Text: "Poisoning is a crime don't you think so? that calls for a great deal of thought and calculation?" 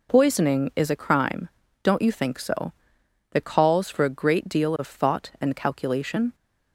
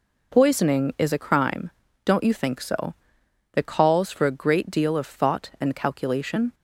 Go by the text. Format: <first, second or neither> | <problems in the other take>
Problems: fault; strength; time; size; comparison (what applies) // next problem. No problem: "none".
neither | pauses between "crime" and "don't"; slight; the same in both